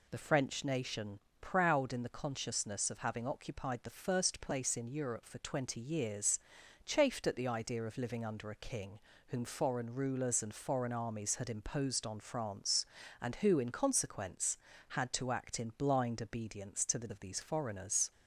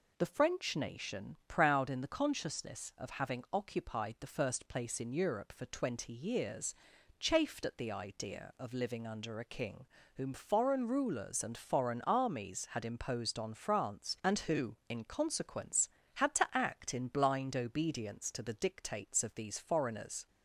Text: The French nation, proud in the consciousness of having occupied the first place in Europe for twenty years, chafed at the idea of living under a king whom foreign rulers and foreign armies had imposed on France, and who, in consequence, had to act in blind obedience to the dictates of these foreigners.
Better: second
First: pauses between "king" and "whom"; slight; at 8.9 s; 0.28 s long // skips "dictates"; at 17.0 s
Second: pauses between "king" and "whom"; slight; at 9.8 s; 0.28 s long

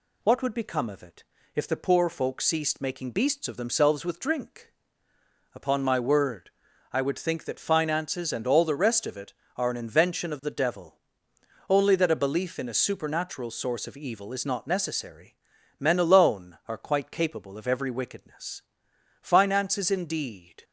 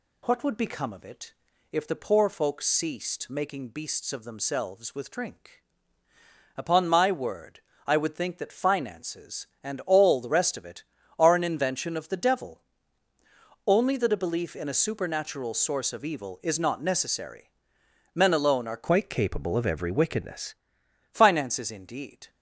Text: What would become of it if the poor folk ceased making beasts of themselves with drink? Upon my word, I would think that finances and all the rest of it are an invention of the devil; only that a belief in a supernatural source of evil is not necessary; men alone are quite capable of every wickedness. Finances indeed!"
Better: first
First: pauses between "it" and "if"; slight; at 1.2 s; 0.32 s long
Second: pauses between "it" and "if"; slight; at 1.3 s; 0.36 s long // changes voice from "quite" to "wickedness"; from 18.8 to 20.5 s; 1.7 s long

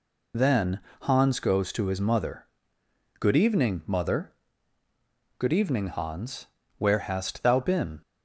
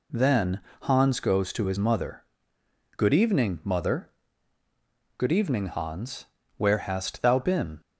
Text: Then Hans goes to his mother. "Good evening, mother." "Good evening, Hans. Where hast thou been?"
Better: second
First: loses the start of "Then"; at 0.3 s; 50 ms // pauses between "Then" and "Hans"; slight; at 0.7 s; 0.24 s long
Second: pauses between "Then" and "Hans"; slight; at 0.5 s; 0.24 s long

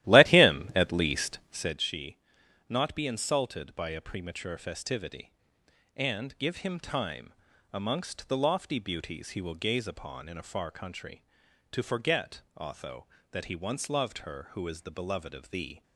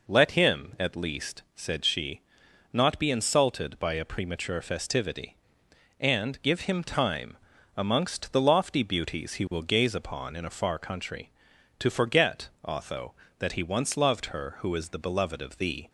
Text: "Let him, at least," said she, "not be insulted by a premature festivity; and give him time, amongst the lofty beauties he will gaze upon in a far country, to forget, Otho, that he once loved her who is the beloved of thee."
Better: second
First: starts louder than the rest; strong; until 1.8 s; 14.5 dB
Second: none

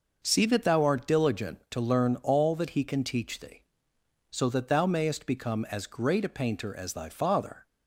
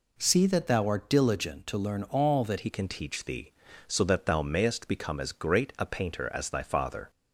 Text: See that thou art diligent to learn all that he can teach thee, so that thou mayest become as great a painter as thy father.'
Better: first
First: none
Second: changes voice at "he"; from 2.5 s on; 4.5 s long

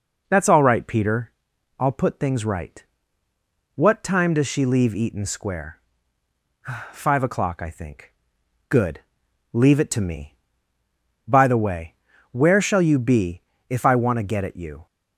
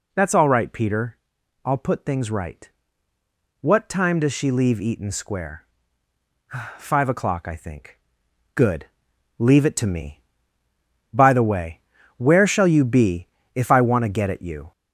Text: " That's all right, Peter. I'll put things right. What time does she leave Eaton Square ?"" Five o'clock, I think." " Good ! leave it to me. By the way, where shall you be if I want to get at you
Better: first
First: pauses between "be" and "if"; slight; at 13.4 s; 0.28 s long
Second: gets louder; noticeable; throughout; 4 dB // pauses between "be" and "if"; slight; at 13.2 s; 0.28 s long

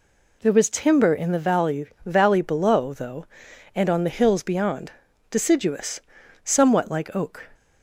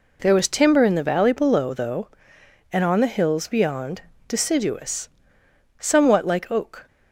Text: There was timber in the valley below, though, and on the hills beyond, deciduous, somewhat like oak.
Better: second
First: says "valley" twice; at 2.0 s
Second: none

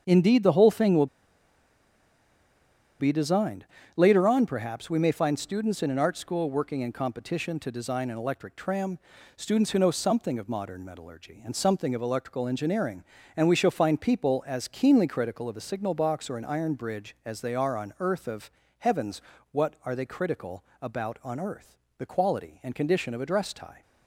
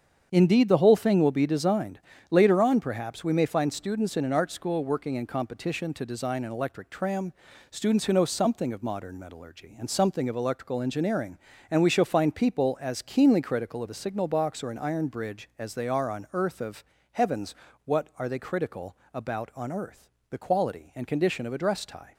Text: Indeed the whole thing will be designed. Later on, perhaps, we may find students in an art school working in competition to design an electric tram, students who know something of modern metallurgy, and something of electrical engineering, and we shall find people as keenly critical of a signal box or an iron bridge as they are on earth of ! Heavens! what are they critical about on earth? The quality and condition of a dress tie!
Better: second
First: starts louder than the rest; strong; until 1.0 s; 7.5 dB // pauses between "will" and "be"; strong; at 1.0 s; 1.9 s long // pauses between "critical" and "about"; slight; at 20.6 s; 0.18 s long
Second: starts louder than the rest; strong; until 1.3 s; 7.5 dB // pauses between "critical" and "about"; slight; at 18.9 s; 0.18 s long

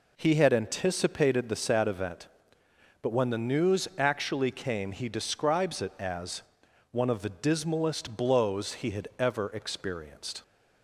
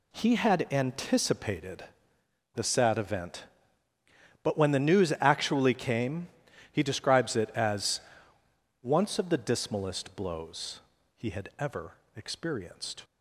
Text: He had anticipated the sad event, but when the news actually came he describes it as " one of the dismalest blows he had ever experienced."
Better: first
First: none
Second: pauses between "anticipated" and "the"; noticeable; at 1.8 s; 0.70 s long // pauses between "came" and "he"; noticeable; at 6.2 s; 0.46 s long // says "once" for "one"; at 8.8 s // pauses between "blows" and "he"; at 10.7 s; 0.38 s long // pauses between "ever" and "experienced"; slight; at 11.9 s; 0.20 s long

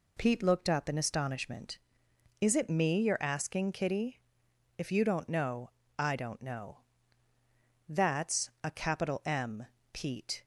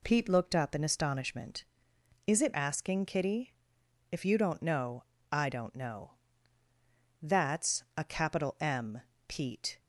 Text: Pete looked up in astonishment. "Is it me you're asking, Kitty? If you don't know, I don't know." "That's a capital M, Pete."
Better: first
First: none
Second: skips "me you're"; at 2.5 s

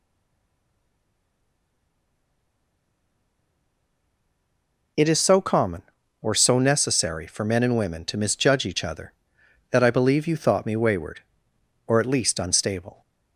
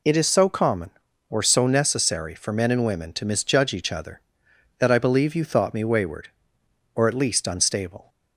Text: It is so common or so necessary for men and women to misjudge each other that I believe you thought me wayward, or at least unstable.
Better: second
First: stays silent before the first word; strong; until 4.9 s; 4.9 s long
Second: none

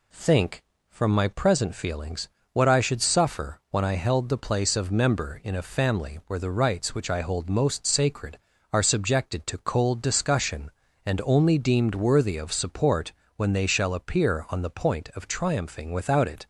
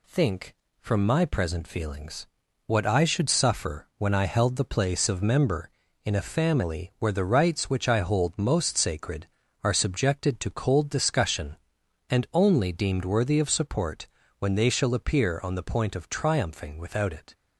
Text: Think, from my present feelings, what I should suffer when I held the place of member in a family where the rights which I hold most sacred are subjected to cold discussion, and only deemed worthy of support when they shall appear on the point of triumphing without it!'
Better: neither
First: pauses between "support" and "when"; slight; at 13.1 s; 0.24 s long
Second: pauses between "support" and "when"; slight; at 14.0 s; 0.32 s long

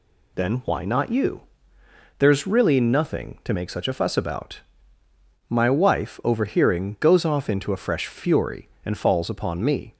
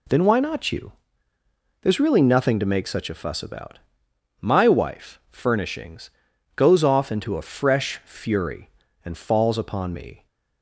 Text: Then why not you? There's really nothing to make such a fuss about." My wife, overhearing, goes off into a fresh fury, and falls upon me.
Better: first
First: none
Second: says "furnishings" for "overhearing"; at 5.3 s

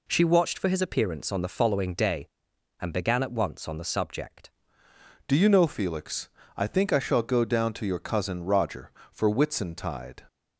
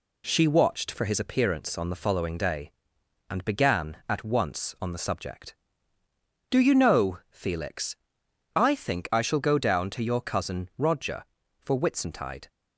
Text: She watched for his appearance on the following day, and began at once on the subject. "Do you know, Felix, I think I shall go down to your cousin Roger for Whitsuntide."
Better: second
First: changes voice at "Do"; from 5.2 s on; 5.0 s long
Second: none

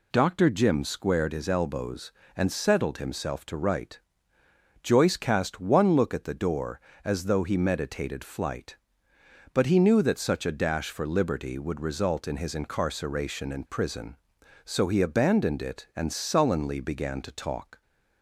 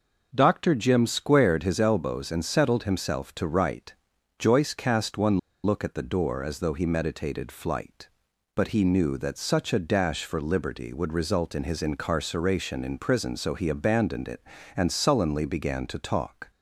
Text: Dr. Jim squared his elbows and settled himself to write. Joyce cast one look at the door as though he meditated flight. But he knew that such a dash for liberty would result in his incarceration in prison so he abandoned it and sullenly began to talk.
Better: first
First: none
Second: pauses between "one" and "look"; slight; at 5.3 s; 0.24 s long

